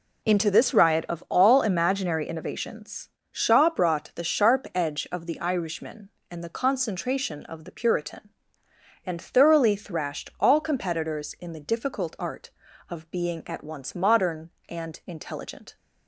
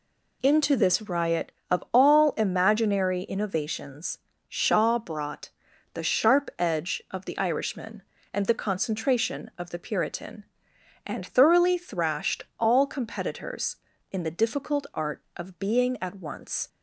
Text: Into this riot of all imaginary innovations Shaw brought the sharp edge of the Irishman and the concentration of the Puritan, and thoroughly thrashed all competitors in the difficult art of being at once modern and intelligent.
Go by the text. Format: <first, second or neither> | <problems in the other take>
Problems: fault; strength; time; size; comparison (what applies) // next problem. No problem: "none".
first | pauses between "innovations" and "Shaw"; slight; at 4.1 s; 0.30 s long; slight in the first // pauses between "brought" and "the"; at 5.4 s; 0.44 s long // stops before "modern and intelligent"; at 16.6 s